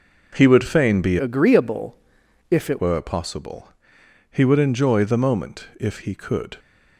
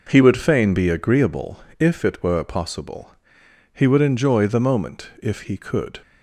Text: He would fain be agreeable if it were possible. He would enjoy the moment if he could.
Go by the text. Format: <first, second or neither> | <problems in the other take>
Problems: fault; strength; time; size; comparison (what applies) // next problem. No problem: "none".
second | changes voice from "agreeable" to "it"; from 1.1 to 2.7 s; 1.6 s long // pauses between "agreeable" and "if"; noticeable; at 1.9 s; 0.56 s long; slight in the second